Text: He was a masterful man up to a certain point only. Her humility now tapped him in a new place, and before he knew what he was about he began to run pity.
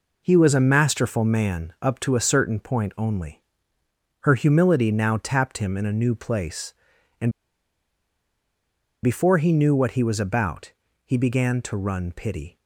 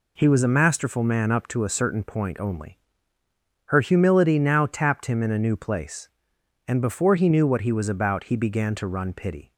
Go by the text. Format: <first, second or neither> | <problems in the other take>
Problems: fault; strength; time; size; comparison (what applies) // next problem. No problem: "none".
second | pauses between "and" and "before"; strong; at 7.2 s; 1.7 s long // pauses between "about" and "he"; slight; at 10.7 s; 0.32 s long